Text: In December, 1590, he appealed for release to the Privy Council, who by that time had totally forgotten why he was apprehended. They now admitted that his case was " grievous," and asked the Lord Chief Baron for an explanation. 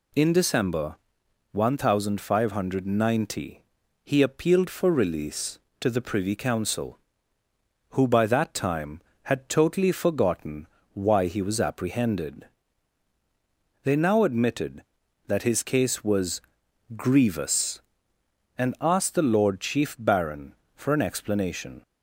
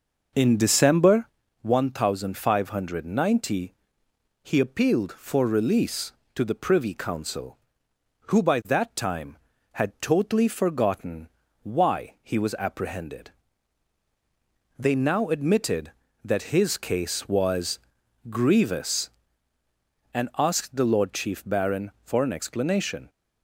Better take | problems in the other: first | starts louder than the rest; noticeable; until 1.4 s; 6 dB // pauses between "forgotten" and "why"; slight; at 11.2 s; 0.36 s long; slight in the first

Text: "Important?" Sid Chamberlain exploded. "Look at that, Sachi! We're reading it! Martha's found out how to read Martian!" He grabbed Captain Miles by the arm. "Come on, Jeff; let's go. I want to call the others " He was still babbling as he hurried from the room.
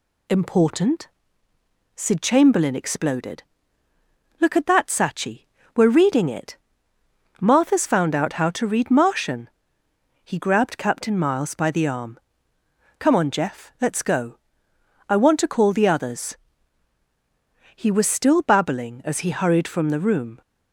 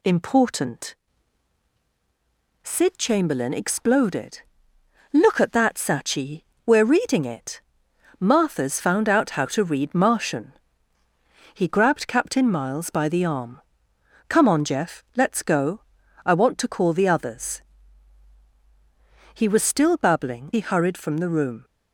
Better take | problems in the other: first | skips "as"; at 20.5 s

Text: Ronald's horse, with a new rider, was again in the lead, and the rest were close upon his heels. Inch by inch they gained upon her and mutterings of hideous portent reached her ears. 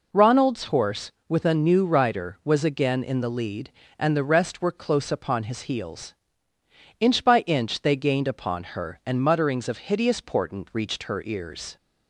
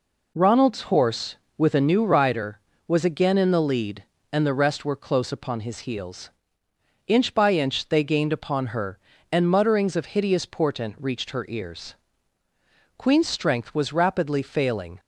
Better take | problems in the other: first | goes on to say "Queen's strength was rapidly failing"; strong; from 12.9 s on; 2.0 s long

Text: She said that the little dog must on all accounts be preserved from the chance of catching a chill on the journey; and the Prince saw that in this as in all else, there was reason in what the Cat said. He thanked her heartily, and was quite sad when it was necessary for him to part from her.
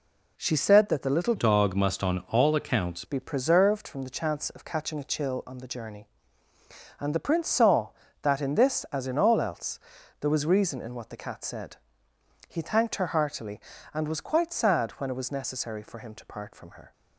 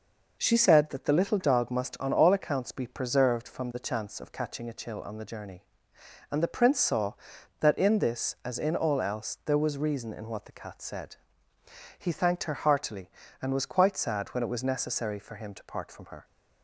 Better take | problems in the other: second | changes voice from "dog" to "accounts"; from 1.3 to 3.0 s; 1.7 s long

